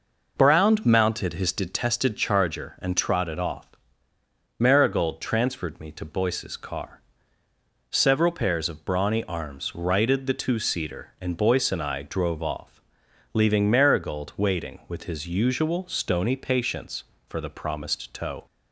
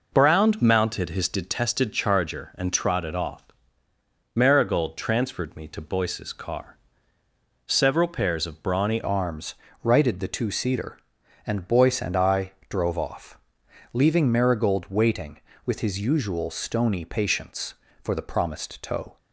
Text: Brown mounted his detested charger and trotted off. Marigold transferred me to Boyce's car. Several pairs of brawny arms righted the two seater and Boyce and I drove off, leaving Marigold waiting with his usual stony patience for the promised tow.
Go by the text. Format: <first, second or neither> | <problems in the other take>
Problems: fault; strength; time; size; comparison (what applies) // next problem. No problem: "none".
first | changes voice at "arms"; from 9.0 s on; 10.1 s long // pauses between "arms" and "righted"; slight; at 9.5 s; 0.28 s long // pauses between "I" and "drove"; slight; at 12.5 s; 0.18 s long